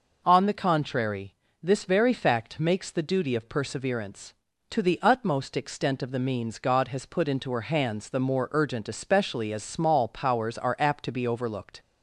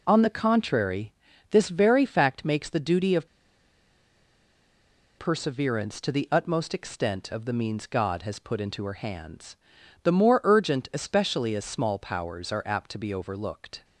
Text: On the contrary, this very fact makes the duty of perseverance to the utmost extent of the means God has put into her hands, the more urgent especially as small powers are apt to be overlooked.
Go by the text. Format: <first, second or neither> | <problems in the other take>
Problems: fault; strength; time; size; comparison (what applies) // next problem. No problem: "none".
first | pauses between "of" and "perseverance"; strong; at 3.2 s; 1.9 s long